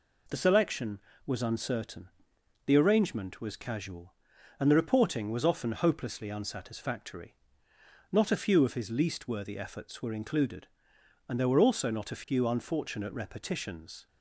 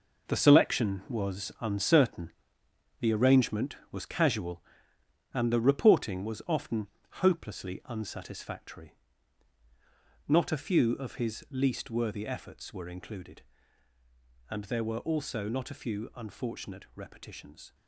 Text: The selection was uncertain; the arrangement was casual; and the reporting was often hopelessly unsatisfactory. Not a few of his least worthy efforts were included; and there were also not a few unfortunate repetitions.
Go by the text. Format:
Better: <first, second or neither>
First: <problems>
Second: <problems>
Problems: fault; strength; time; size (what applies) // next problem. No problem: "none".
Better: first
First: none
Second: gets quieter; strong; throughout; 10 dB // pauses between "often" and "hopelessly"; slight; at 6.8 s; 0.34 s long